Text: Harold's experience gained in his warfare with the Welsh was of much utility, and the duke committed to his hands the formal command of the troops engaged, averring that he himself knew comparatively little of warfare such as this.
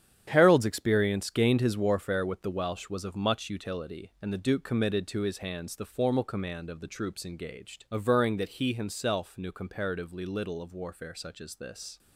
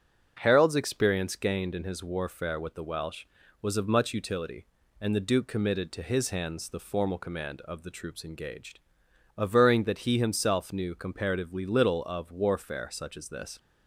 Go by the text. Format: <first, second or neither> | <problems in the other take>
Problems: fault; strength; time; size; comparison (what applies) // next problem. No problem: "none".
second | starts louder than the rest; strong; until 1.2 s; 9.5 dB; noticeable in the second // skips "in"; at 1.6 s